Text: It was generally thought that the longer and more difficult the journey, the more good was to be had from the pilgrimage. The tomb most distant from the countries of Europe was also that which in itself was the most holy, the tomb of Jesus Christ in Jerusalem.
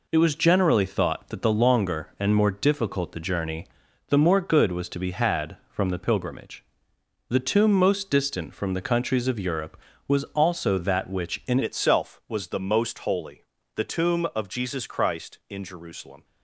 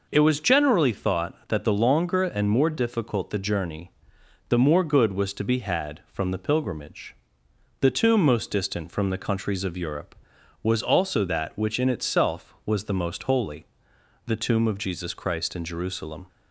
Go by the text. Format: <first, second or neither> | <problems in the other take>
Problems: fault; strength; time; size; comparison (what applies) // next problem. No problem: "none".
second | changes voice at "itself"; from 11.6 s on; 4.6 s long